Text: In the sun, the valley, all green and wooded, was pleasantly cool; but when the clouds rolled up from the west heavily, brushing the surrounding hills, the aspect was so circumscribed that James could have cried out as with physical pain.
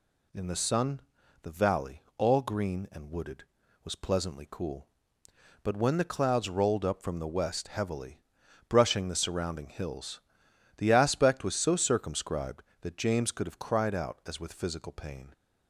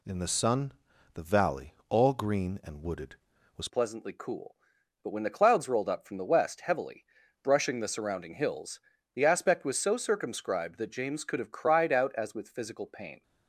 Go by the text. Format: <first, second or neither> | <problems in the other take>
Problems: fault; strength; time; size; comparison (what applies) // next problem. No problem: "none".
first | changes voice at "pleasantly"; from 3.6 s on; 9.6 s long